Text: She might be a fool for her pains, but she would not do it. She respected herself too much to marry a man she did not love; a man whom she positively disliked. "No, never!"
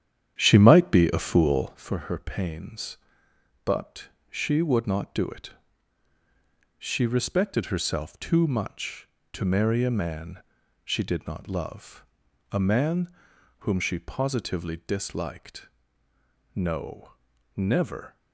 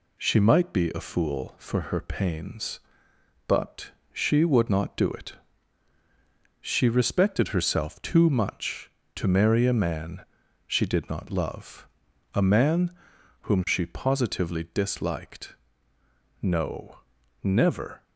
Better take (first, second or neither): second